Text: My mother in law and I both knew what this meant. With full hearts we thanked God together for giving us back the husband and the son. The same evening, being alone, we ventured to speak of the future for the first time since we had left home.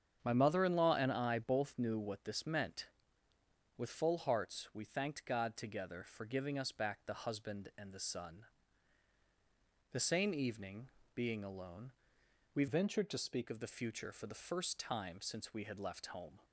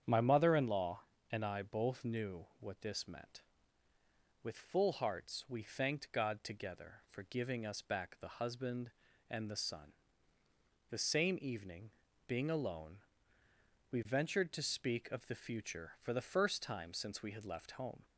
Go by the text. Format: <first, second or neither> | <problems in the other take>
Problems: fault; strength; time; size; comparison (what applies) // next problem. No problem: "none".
second | starts louder than the rest; strong; until 1.2 s; 8 dB; strong in the second // changes voice from "ventured" to "speak"; from 12.6 to 13.4 s; 0.8 s long